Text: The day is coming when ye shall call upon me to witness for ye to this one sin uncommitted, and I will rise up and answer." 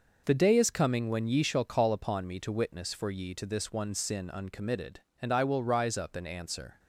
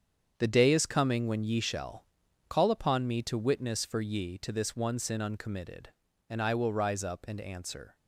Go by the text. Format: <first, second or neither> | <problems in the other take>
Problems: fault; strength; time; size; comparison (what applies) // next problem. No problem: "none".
first | gets quieter; strong; throughout; 10 dB // pauses between "shall" and "call"; noticeable; at 2.0 s; 0.46 s long